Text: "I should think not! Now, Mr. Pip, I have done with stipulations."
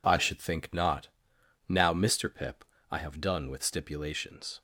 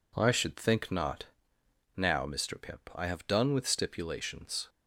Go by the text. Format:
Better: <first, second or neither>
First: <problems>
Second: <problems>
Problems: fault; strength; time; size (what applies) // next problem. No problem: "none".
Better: neither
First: none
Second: none